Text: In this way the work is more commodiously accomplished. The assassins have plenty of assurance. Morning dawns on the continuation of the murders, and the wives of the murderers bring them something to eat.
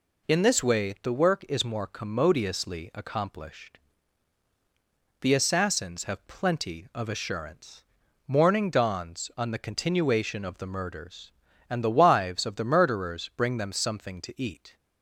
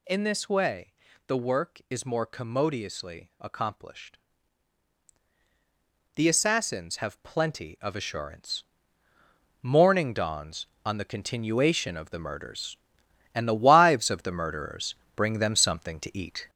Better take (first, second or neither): first